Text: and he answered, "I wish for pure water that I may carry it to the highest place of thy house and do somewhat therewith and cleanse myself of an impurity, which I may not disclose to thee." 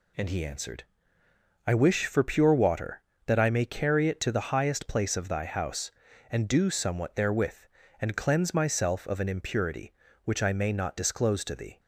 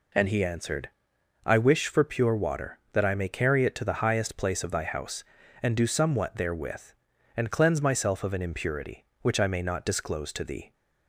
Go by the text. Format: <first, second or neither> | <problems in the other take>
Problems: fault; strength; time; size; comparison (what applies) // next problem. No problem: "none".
neither | none